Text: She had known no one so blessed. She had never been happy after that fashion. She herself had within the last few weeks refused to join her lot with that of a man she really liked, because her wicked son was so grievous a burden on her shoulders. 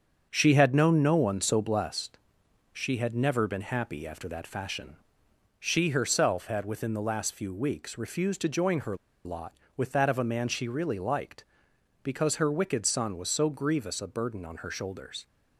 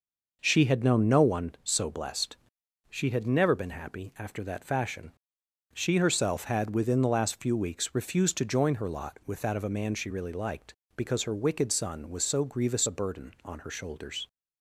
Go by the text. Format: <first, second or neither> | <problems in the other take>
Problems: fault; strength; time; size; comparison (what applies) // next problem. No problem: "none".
second | starts louder than the rest; until 1.3 s; 7 dB // pauses between "her" and "lot"; slight; at 8.9 s; 0.30 s long